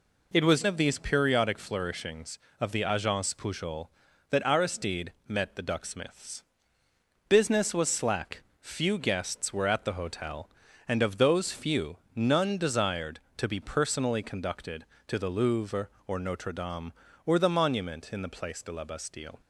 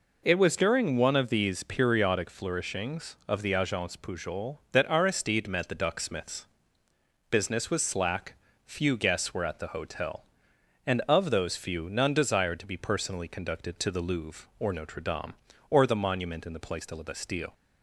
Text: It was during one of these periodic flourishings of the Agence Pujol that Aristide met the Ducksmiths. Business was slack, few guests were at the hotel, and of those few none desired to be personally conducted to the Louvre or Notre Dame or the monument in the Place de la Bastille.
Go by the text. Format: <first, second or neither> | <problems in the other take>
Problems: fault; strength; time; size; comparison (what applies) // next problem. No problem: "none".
second | skips "during one"; at 0.6 s // pauses between "Aristide" and "met"; slight; at 5.1 s; 0.16 s long // pauses between "few" and "none"; slight; at 11.9 s; 0.20 s long